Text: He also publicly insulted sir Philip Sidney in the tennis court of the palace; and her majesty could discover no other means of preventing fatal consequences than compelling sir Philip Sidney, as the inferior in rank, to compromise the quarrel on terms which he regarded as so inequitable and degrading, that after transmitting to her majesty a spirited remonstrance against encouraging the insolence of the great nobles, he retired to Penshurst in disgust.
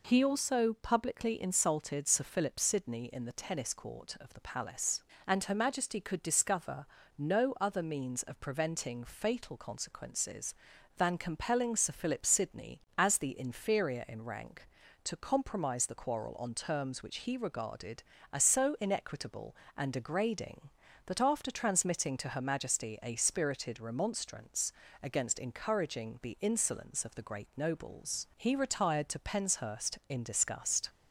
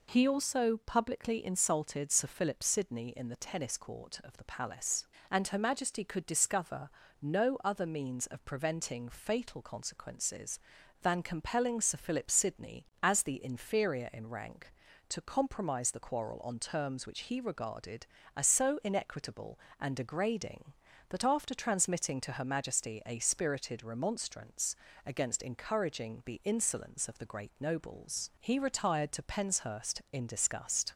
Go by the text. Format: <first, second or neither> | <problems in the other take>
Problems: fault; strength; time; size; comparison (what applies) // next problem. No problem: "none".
neither | pauses between "discover" and "no"; slight; the same in both // pauses between "remonstrance" and "against"; slight; the same in both